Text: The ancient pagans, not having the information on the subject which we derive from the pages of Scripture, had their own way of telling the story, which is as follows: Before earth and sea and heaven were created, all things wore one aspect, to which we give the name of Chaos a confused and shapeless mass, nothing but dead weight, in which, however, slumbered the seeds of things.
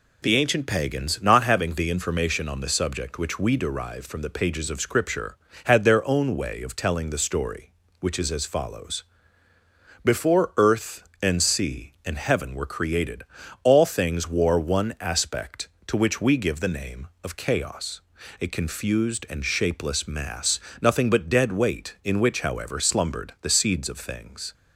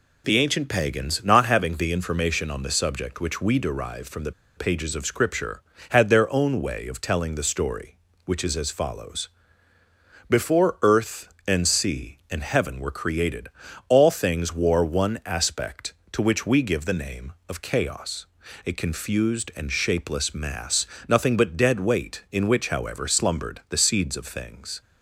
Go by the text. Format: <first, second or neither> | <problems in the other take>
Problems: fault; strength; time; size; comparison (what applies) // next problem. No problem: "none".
first | pauses between "the" and "pages"; slight; at 4.3 s; 0.25 s long // pauses between "Chaos" and "a"; at 18.2 s; 0.40 s long; also in the first